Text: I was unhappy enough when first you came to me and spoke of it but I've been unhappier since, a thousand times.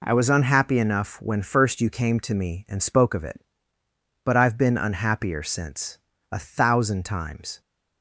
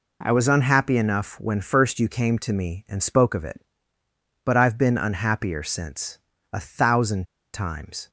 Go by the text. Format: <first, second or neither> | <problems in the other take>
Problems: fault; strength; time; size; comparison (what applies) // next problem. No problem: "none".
first | pauses between "thousand" and "times"; slight; at 7.2 s; 0.28 s long